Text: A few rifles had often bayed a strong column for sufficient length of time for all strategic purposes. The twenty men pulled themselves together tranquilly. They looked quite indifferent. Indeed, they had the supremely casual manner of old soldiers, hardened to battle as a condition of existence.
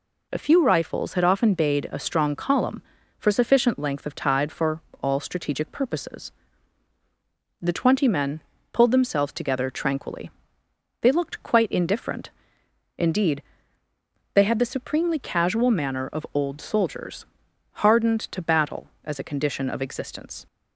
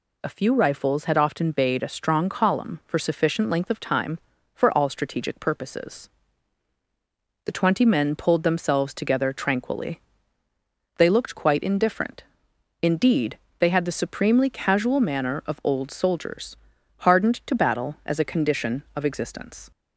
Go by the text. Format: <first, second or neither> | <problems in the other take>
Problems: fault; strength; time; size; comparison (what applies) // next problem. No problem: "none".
second | says "tide" for "time"; at 4.1 s // pauses between "for" and "all"; slight; at 4.8 s; 0.18 s long // pauses between "men" and "pulled"; slight; at 8.4 s; 0.30 s long